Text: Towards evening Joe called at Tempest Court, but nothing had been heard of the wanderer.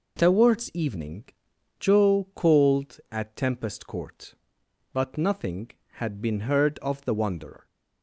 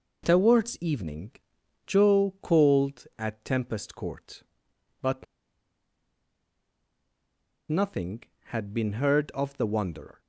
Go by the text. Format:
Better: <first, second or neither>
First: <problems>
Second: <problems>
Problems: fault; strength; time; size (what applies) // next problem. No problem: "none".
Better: first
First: pauses between "evening" and "Joe"; noticeable; at 1.2 s; 0.54 s long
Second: pauses between "evening" and "Joe"; noticeable; at 1.3 s; 0.54 s long // pauses between "but" and "nothing"; strong; at 5.2 s; 2.4 s long